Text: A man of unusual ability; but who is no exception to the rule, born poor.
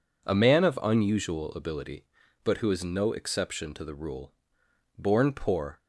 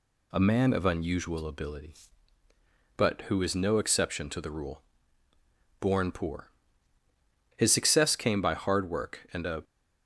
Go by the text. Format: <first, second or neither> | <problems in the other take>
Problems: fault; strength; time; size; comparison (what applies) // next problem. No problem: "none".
first | goes on to say "His success came by hard work and a"; strong; from 7.5 s on; 2.0 s long